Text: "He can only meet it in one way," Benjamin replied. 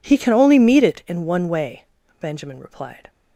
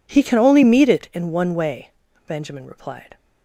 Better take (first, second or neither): neither